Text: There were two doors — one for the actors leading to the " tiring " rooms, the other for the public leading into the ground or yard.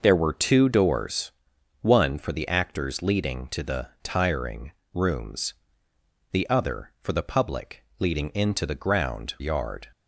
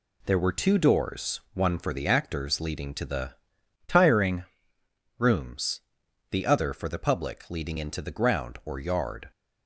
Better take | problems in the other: second | skips "or"; at 9.3 s

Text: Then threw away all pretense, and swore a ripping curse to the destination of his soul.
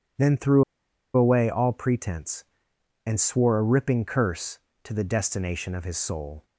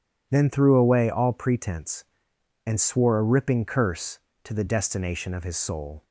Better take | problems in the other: second | pauses between "threw" and "away"; noticeable; at 0.6 s; 0.53 s long

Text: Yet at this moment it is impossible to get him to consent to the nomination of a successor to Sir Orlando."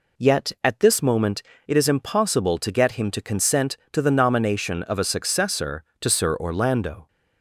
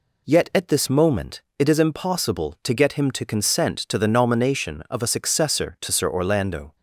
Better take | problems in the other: neither | pauses between "moment" and "it"; slight; the same in both

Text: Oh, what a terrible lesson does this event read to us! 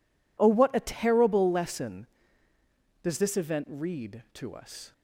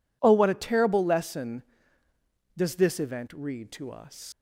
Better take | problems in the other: first | leaves "us" unfinished; at 4.3 s; 115 ms

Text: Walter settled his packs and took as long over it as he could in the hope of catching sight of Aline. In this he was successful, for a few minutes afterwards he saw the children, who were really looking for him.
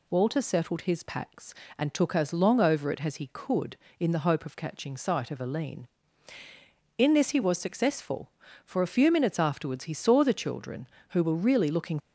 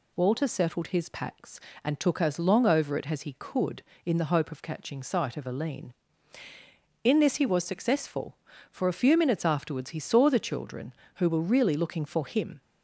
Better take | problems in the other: second | stops before "for him"; at 11.9 s

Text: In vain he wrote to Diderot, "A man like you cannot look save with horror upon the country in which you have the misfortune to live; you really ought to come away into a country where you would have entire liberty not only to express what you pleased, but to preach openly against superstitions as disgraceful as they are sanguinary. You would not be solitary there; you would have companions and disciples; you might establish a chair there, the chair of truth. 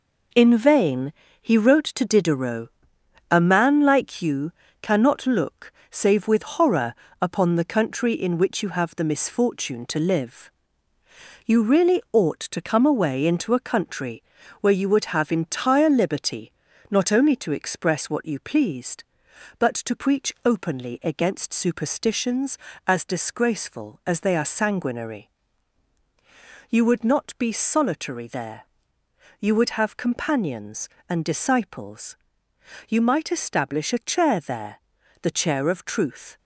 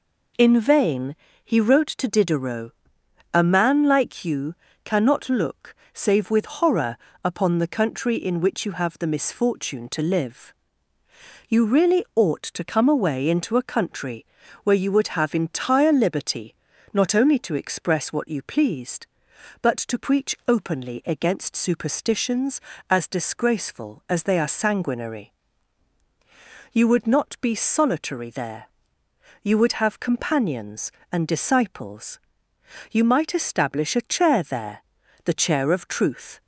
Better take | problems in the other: second | gets quieter; throughout; 6 dB // pauses between "vain" and "he"; slight; at 1.1 s; 0.28 s long; slight in the second // pauses between "you" and "cannot"; slight; at 4.5 s; 0.28 s long; slight in the second // pauses between "look" and "save"; slight; at 5.7 s; 0.18 s long; slight in the second // pauses between "horror" and "upon"; slight; at 6.9 s; 0.26 s long; slight in the second // pauses between "country" and "where"; at 14.2 s; 0.40 s long; also in the second // pauses between "liberty" and "not"; at 16.4 s; 0.40 s long; also in the second

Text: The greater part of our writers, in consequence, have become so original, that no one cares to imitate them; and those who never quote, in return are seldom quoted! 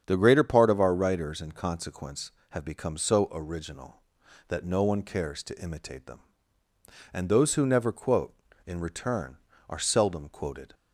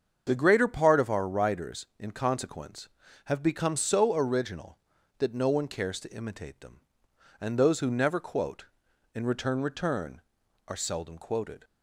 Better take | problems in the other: first | starts louder than the rest; strong; until 1.2 s; 7 dB; strong in the first // says "return" twice; at 9.6 s

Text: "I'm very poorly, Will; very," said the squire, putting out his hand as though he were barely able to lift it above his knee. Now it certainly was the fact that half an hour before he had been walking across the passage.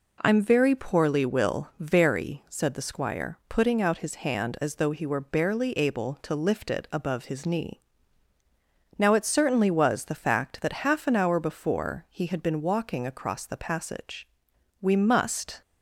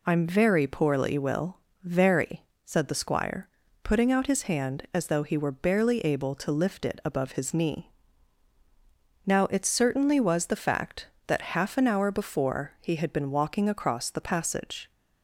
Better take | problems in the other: second | goes on to say "We must"; noticeable; from 14.8 s on; 0.80 s long

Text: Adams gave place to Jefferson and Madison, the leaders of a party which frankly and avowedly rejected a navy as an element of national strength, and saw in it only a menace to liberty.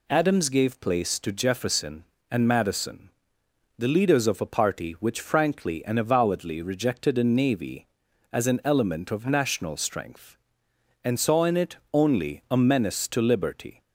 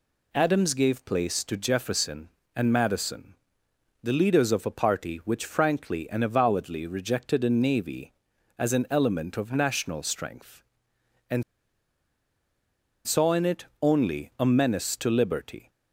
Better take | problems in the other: first | pauses between "and" and "saw"; strong; at 11.4 s; 1.6 s long // pauses between "it" and "only"; slight; at 13.6 s; 0.18 s long; slight in the first

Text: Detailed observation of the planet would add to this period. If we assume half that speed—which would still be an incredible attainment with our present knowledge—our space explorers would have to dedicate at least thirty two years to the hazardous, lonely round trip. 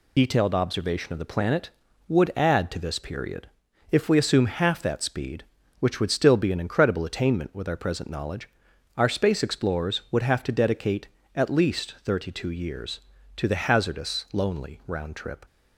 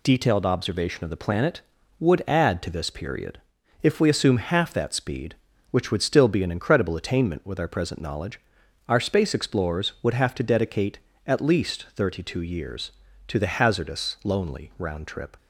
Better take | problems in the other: second | loses the start of "Detailed"; at 0.1 s; 40 ms

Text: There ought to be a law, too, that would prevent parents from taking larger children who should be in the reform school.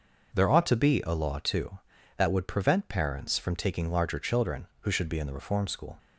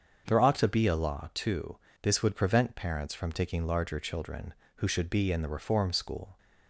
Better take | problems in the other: first | starts louder than the rest; until 1.2 s; 7 dB // says "this" for "that"; at 2.0 s

